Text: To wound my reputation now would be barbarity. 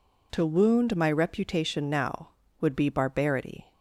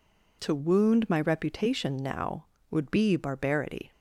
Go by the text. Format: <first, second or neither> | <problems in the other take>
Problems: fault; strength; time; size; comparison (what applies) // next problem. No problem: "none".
neither | none